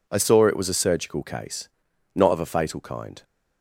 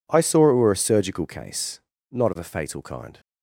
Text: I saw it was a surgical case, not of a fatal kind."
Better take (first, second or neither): first